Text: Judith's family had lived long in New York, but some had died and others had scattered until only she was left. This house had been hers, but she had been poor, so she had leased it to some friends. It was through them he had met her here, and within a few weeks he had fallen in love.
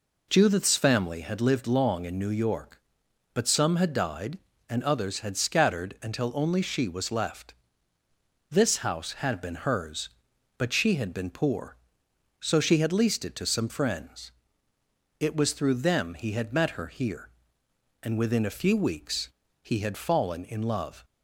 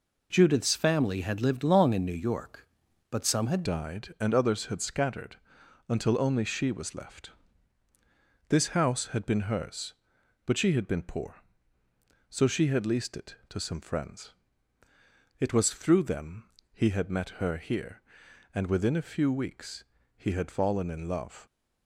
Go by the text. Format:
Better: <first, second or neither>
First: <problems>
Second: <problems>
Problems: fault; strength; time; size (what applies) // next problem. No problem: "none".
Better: first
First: pauses between "weeks" and "he"; slight; at 19.3 s; 0.32 s long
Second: changes voice at "died"; from 3.6 s on; 17.8 s long // pauses between "scattered" and "until"; noticeable; at 5.3 s; 0.54 s long // pauses between "them" and "he"; slight; at 16.4 s; 0.22 s long // pauses between "weeks" and "he"; slight; at 19.8 s; 0.32 s long